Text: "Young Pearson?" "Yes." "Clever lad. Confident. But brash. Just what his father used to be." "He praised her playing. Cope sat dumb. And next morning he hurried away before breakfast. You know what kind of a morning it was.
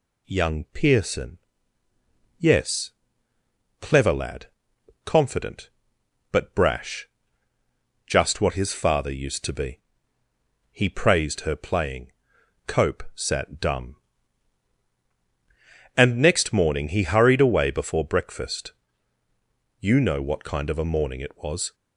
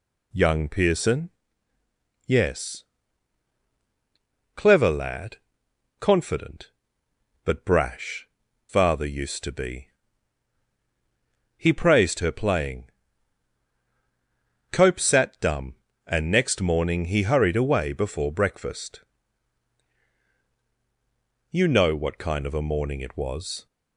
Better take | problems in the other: first | skips "Just what his"; at 8.4 s

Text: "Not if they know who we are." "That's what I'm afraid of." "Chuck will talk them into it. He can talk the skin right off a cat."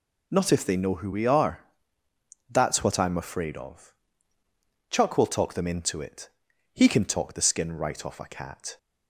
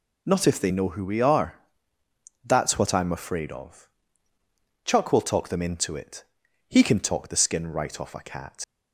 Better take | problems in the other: first | leaves "cat" unfinished; at 8.6 s; 80 ms

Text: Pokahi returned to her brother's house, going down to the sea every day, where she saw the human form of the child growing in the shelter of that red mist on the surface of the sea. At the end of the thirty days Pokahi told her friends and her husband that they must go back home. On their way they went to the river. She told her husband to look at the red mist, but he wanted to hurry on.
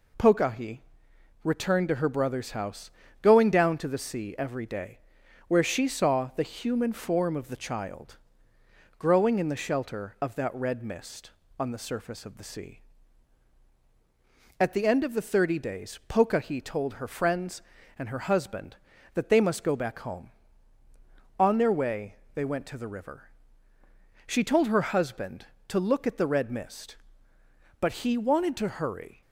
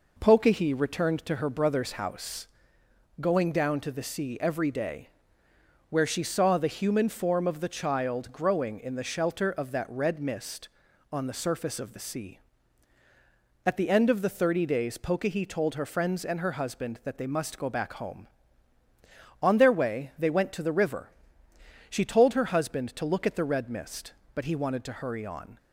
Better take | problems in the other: second | pauses between "Pokahi" and "returned"; noticeable; at 0.7 s; 0.64 s long // pauses between "child" and "growing"; noticeable; at 8.1 s; 0.80 s long // pauses between "way" and "they"; slight; at 22.1 s; 0.20 s long // stops before "on"; at 29.2 s

